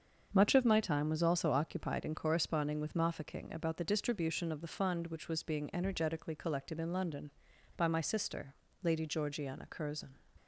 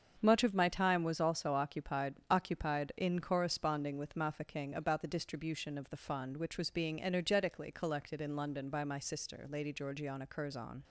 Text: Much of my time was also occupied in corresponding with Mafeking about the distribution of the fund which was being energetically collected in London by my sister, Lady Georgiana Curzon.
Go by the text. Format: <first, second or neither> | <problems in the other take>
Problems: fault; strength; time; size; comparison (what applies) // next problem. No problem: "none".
first | starts louder than the rest; strong; until 1.2 s; 7 dB; also in the first // says "occupied" twice; at 2.2 s